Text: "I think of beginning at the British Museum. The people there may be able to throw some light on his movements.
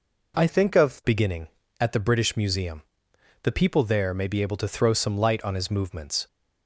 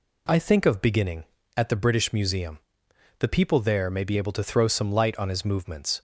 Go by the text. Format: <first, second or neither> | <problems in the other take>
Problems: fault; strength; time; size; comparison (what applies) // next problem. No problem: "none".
second | changes voice from "think" to "of"; from 0.4 to 1.0 s; 0.6 s long